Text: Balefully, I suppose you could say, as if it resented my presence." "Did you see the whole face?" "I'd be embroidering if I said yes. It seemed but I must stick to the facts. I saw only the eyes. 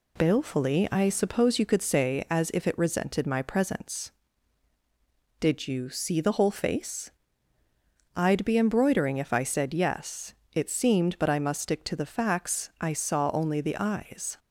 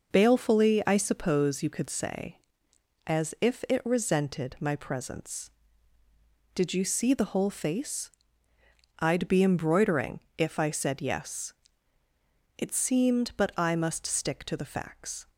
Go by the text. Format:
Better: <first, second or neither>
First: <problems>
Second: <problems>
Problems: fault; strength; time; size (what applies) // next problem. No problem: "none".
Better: first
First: none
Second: pauses between "embroidering" and "if"; slight; at 10.1 s; 0.16 s long // stops before "I saw only the eyes"; at 15.2 s